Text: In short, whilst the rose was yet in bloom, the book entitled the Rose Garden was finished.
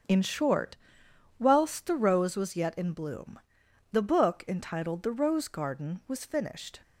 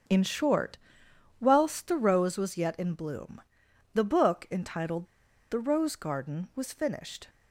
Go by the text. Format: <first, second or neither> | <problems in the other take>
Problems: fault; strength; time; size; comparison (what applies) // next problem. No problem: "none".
first | starts louder than the rest; until 1.7 s; 6.5 dB; strong in the first // pauses between "entitled" and "the"; at 5.0 s; 0.45 s long